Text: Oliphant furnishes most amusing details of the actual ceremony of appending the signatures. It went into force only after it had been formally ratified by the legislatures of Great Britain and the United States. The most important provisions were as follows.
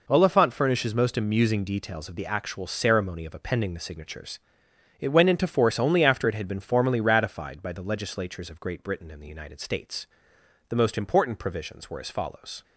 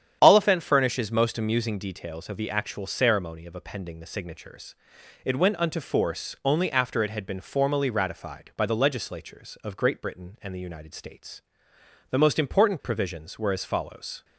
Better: first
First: none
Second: starts louder than the rest; strong; until 1.2 s; 9 dB // says "unto" for "into"; at 5.5 s

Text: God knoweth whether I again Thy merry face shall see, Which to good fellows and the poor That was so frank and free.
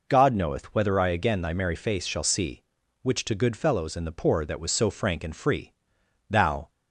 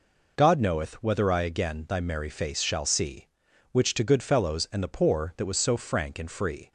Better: second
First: goes on to say "Thou"; slight; from 6.2 s on; 0.40 s long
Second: none

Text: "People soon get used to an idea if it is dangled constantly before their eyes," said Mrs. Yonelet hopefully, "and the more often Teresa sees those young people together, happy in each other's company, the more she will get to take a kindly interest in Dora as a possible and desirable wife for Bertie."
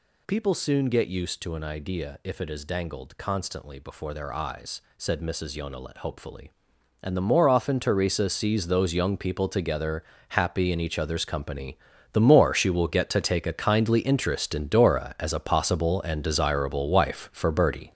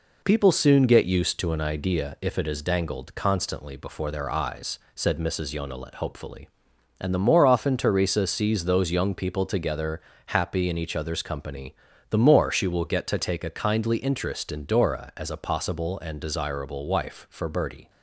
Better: second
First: gets louder; strong; throughout; 7.5 dB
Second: none

